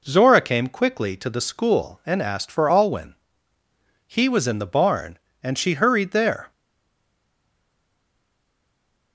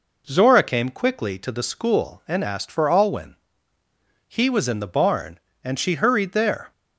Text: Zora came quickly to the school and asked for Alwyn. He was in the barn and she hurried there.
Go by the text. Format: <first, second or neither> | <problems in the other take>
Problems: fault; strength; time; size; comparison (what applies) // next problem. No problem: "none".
second | stays silent after the last word; strong; from 6.5 s on; 2.6 s long